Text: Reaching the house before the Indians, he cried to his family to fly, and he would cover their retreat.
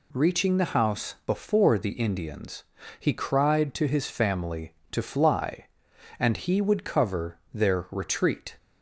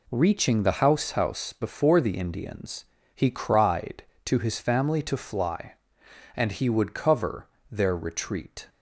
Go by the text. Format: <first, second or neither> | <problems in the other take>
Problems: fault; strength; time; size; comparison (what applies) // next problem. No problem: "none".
first | says "house" twice; at 1.1 s // pauses between "cover" and "their"; slight; at 7.4 s; 0.24 s long; slight in the first